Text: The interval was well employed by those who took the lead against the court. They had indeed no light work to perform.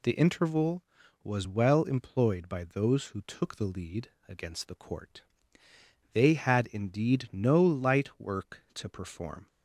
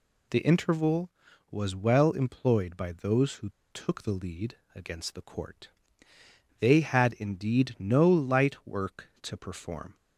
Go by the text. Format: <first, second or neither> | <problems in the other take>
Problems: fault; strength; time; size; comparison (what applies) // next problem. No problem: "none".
first | pauses between "who" and "took"; slight; at 3.4 s; 0.22 s long // pauses between "lead" and "against"; slight; at 4.5 s; 0.18 s long; slight in the first